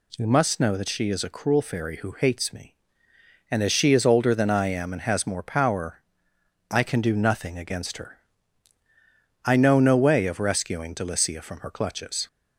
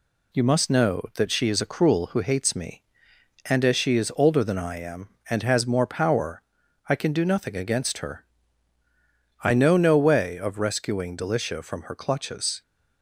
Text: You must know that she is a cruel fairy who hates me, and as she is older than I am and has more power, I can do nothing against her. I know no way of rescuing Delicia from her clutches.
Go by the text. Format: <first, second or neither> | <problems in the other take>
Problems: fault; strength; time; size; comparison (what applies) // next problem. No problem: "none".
first | skips "fairy"; at 2.0 s